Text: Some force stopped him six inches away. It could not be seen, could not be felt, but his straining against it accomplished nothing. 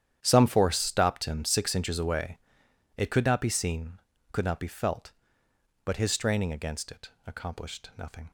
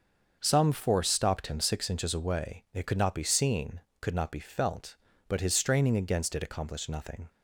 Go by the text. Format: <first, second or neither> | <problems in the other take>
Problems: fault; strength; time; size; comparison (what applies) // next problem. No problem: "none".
second | gets quieter; strong; throughout; 16.5 dB // starts louder than the rest; strong; until 1.2 s; 10 dB; also in the second // pauses between "it" and "accomplished"; slight; at 7.1 s; 0.16 s long